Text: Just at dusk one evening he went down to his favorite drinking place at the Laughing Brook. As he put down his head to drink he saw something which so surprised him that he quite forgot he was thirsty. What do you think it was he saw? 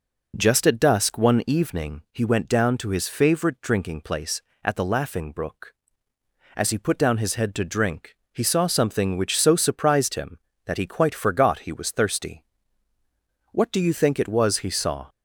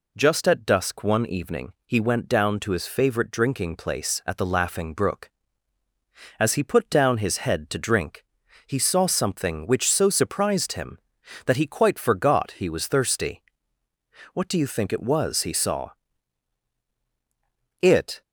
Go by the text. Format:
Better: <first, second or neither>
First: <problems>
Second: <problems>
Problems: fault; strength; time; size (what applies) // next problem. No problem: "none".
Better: first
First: pauses between "drink" and "he"; slight; at 8.1 s; 0.16 s long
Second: pauses between "drink" and "he"; at 8.2 s; 0.42 s long // goes on to say "It"; slight; from 17.8 s on; 0.40 s long